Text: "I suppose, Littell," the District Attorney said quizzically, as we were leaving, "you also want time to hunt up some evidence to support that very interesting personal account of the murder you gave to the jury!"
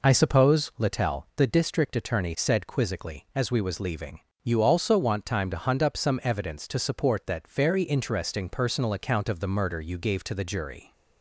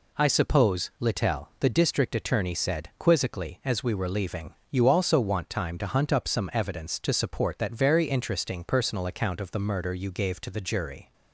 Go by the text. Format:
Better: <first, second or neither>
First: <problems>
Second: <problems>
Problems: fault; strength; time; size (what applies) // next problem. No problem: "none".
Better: second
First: says "was" for "were"; at 3.6 s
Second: none